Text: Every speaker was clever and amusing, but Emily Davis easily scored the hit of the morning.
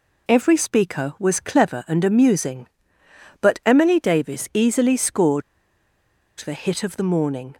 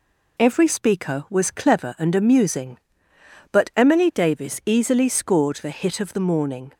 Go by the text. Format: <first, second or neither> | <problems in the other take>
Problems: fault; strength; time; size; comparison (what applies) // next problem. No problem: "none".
second | pauses between "scored" and "the"; at 5.4 s; 0.98 s long